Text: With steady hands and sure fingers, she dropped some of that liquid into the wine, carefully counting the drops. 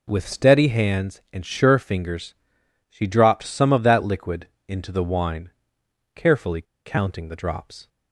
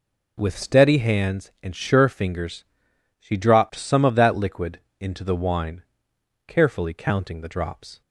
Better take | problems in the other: second | pauses between "liquid" and "into"; slight; at 4.4 s; 0.20 s long; slight in the second // pauses between "carefully" and "counting"; slight; at 6.6 s; 0.22 s long

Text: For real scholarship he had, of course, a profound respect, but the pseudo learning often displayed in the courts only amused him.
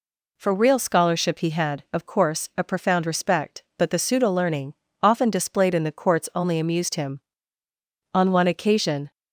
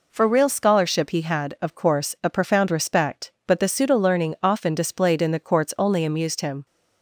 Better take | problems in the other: second | pauses between "learning" and "often"; slight; at 4.7 s; 0.28 s long // goes on to say "On one occasion"; noticeable; from 8.1 s on; 0.98 s long

